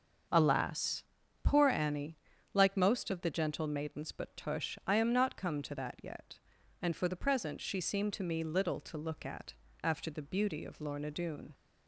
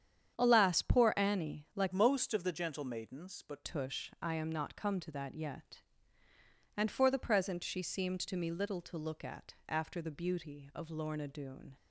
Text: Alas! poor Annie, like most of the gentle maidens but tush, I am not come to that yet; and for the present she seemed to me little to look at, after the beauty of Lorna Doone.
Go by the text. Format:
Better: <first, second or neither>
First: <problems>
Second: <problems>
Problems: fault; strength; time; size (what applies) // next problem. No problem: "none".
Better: first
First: starts louder than the rest; until 1.6 s; 6.5 dB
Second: starts louder than the rest; strong; until 1.3 s; 9 dB // changes voice from "most" to "but"; from 1.9 to 3.6 s; 1.7 s long